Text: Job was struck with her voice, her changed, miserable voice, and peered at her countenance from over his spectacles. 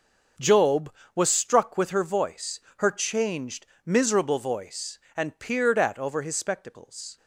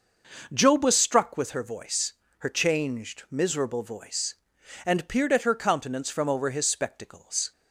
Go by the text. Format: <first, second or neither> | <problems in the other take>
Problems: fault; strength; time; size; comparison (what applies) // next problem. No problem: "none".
second | starts louder than the rest; until 1.6 s; 6.5 dB // skips "her countenance from"; at 5.9 s